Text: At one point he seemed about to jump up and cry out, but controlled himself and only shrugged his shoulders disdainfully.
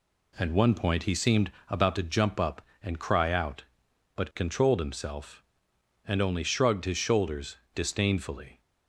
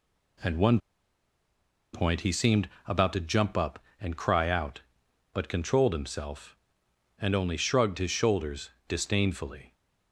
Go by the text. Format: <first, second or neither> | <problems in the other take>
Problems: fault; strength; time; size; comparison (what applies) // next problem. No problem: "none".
first | pauses between "one" and "point"; at 0.7 s; 1.1 s long // pauses between "seemed" and "about"; slight; at 2.6 s; 0.16 s long; slight in the first // pauses between "shoulders" and "disdainfully"; slight; at 8.6 s; 0.18 s long; slight in the first